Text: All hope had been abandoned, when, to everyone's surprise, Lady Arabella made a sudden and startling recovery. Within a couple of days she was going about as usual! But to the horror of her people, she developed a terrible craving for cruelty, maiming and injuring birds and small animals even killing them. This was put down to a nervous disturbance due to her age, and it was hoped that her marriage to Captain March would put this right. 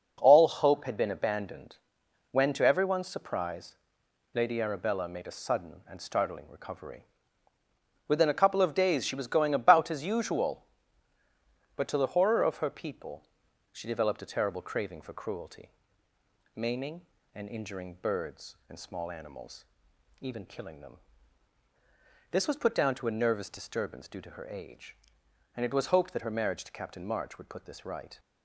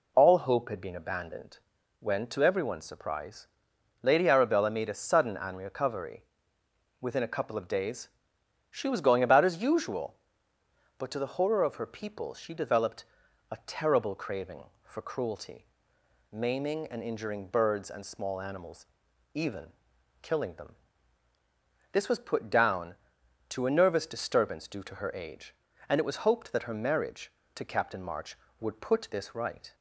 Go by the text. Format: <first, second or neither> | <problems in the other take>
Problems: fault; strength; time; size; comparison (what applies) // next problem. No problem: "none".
first | skips "startling"; at 5.5 s // pauses between "days" and "she"; noticeable; at 8.0 s; 0.62 s long // pauses between "developed" and "a"; noticeable; at 13.0 s; 0.46 s long // pauses between "animals" and "even"; noticeable; at 18.8 s; 0.50 s long; noticeable in the first // pauses between "even" and "killing"; noticeable; at 19.6 s; 0.56 s long